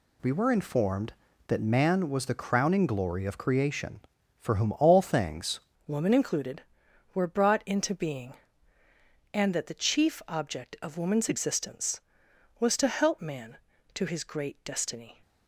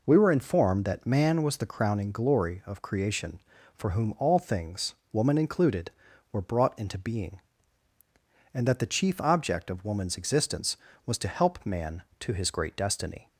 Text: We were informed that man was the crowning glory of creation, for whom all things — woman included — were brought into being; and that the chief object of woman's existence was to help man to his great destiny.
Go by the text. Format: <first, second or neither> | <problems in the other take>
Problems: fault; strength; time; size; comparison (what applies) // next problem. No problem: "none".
second | changes voice at "woman"; from 5.8 s on; 9.4 s long